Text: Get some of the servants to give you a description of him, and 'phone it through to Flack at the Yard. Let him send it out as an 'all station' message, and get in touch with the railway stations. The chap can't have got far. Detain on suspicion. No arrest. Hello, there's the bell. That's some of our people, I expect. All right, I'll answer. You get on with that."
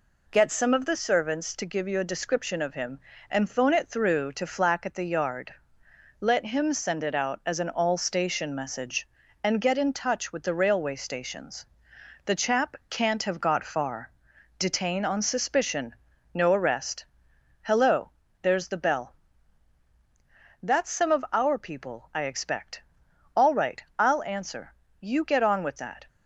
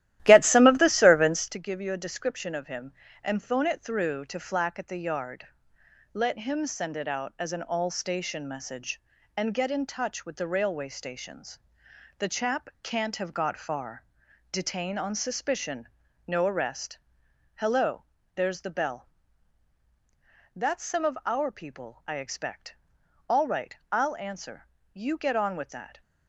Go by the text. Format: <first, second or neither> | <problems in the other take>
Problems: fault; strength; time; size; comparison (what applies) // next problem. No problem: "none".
first | starts louder than the rest; strong; until 1.5 s; 13.5 dB